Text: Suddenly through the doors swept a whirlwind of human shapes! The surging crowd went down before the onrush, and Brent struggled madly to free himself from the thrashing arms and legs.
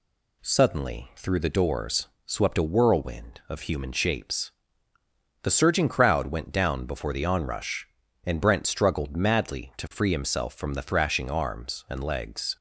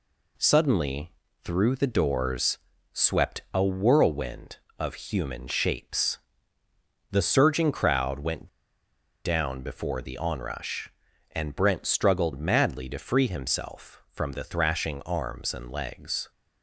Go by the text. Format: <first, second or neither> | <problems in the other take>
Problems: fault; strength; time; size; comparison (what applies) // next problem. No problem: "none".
first | pauses between "Suddenly" and "through"; slight; at 1.1 s; 0.32 s long // pauses between "doors" and "swept"; slight; at 2.5 s; 0.36 s long; slight in the first // pauses between "went" and "down"; noticeable; at 8.4 s; 0.77 s long